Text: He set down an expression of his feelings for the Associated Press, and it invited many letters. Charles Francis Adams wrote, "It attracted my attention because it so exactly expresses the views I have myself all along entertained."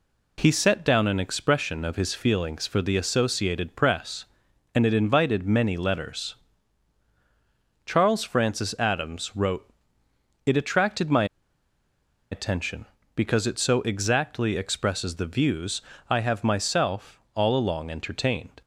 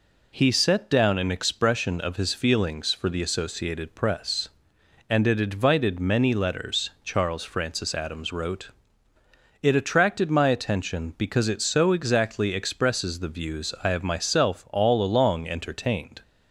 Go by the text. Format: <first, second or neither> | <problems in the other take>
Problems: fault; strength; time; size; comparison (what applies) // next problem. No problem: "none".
second | pauses between "my" and "attention"; at 11.2 s; 1.0 s long // pauses between "views" and "I"; slight; at 15.8 s; 0.28 s long // pauses between "myself" and "all"; slight; at 17.1 s; 0.16 s long